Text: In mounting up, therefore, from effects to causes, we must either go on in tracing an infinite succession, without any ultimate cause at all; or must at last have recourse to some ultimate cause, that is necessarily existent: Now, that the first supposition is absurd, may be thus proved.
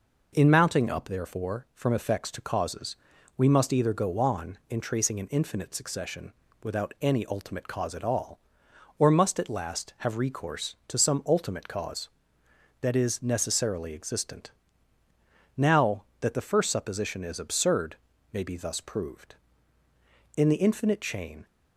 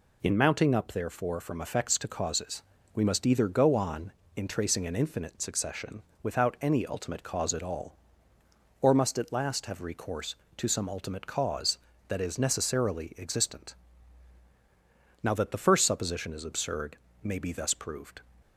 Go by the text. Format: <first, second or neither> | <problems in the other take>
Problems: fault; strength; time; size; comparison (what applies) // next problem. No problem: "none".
second | goes on to say "In the infinite chain"; noticeable; from 20.3 s on; 1.1 s long